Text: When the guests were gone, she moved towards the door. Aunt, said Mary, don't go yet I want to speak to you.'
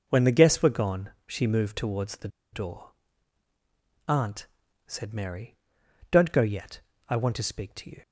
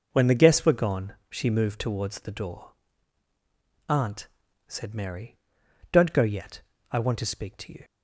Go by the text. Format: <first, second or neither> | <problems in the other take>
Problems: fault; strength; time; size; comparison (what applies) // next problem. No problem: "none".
second | pauses between "the" and "door"; slight; at 2.2 s; 0.25 s long // pauses between "yet" and "I"; slight; at 6.7 s; 0.30 s long; slight in the second